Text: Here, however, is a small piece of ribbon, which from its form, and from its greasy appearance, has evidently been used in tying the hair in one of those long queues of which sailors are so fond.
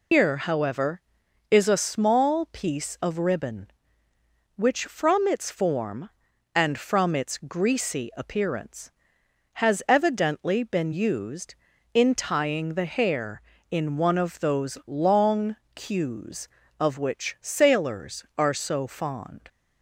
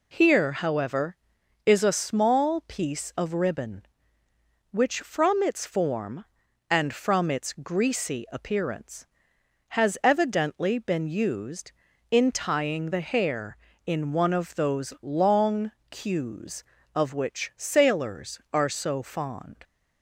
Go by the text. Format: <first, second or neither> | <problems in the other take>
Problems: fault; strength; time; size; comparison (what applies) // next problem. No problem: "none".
second | loses the start of "Here"; at 0.1 s; 155 ms // pauses between "long" and "queues"; slight; at 15.5 s; 0.20 s long; slight in the second